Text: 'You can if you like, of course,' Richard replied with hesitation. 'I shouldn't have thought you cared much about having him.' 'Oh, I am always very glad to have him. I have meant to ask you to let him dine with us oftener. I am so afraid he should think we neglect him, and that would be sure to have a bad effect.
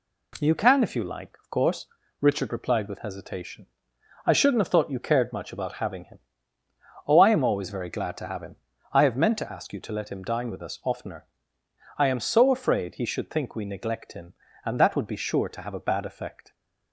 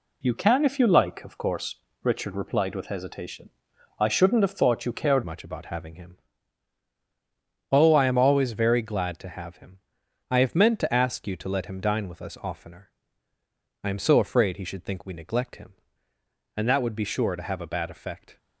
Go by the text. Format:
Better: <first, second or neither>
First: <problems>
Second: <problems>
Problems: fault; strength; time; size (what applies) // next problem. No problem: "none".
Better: first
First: none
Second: changes voice at "much"; from 5.2 s on; 13.1 s long